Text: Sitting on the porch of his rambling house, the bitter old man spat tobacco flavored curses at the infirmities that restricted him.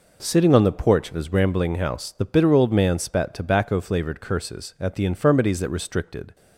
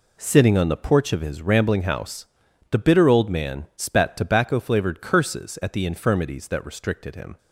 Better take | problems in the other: second | stops before "him"; at 6.3 s

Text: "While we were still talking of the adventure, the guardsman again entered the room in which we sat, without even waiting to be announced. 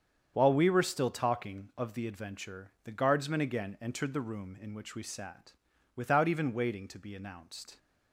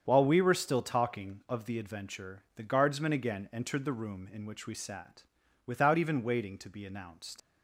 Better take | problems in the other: first | starts louder than the rest; strong; until 1.0 s; 7.5 dB; strong in the first // leaves "announced" unfinished; at 7.3 s; 85 ms

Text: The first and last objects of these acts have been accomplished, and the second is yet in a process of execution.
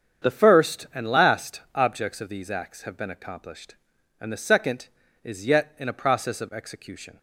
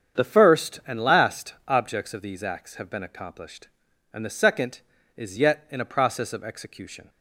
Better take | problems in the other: neither | starts louder than the rest; strong; the same in both

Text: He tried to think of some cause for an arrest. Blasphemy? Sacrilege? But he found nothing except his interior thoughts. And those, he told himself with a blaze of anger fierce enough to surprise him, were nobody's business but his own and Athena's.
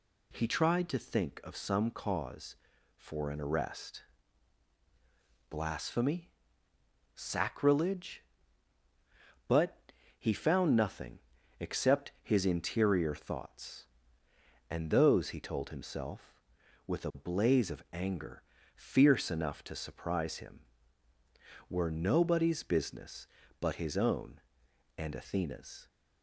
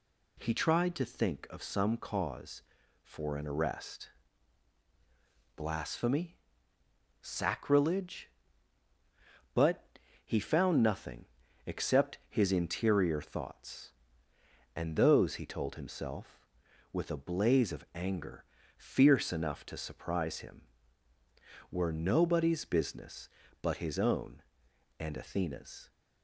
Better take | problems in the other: neither | pauses between "But" and "he"; the same in both // pauses between "nothing" and "except"; the same in both // pauses between "anger" and "fierce"; slight; the same in both

